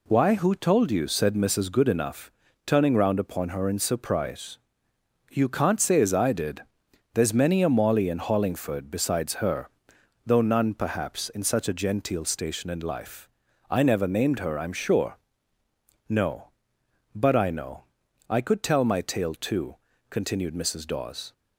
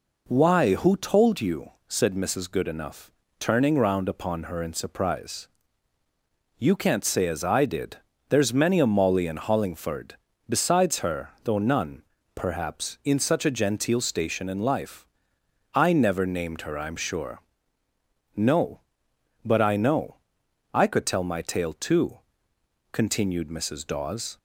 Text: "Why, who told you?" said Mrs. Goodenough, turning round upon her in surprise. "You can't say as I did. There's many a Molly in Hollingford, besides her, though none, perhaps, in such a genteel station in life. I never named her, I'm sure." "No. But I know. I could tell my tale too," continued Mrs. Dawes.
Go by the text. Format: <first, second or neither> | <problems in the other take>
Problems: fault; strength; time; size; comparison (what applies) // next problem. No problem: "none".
neither | none